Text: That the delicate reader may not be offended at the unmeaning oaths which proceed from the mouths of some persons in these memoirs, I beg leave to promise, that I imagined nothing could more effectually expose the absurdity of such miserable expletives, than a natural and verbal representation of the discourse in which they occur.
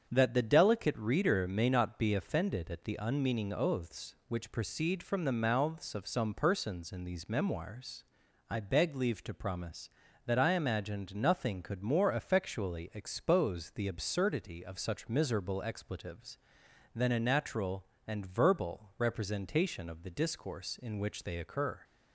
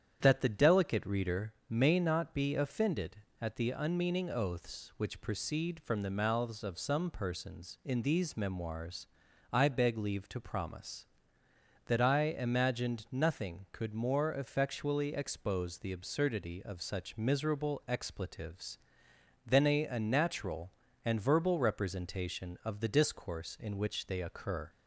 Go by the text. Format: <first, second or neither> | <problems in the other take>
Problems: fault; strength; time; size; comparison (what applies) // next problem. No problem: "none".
first | starts louder than the rest; strong; until 1.2 s; 9 dB; strong in the first // pauses between "reader" and "may"; slight; at 1.5 s; 0.16 s long // says "a" twice; at 19.8 s